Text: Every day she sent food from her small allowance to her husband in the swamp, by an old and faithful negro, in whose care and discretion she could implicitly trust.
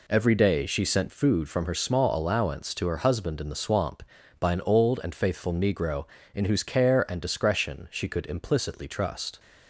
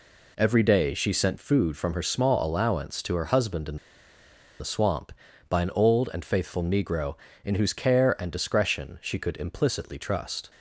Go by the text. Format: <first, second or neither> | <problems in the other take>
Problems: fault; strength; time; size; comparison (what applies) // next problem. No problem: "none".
first | pauses between "in" and "the"; noticeable; at 3.7 s; 0.83 s long